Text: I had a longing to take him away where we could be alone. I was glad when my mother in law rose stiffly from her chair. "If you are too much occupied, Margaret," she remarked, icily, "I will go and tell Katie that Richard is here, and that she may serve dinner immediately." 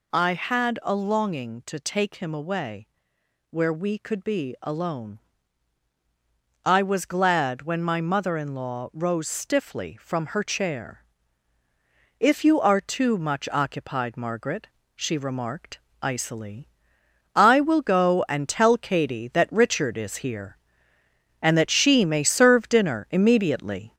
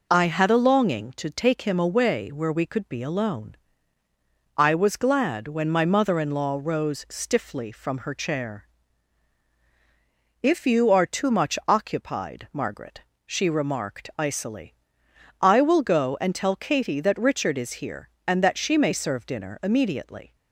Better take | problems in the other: second | gets louder; throughout; 3.5 dB // pauses between "away" and "where"; noticeable; at 2.8 s; 0.62 s long

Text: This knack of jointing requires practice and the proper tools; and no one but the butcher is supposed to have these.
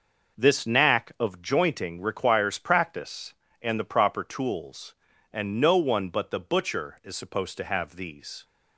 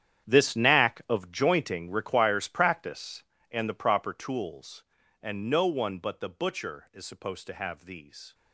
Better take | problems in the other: first | gets quieter; strong; throughout; 14 dB

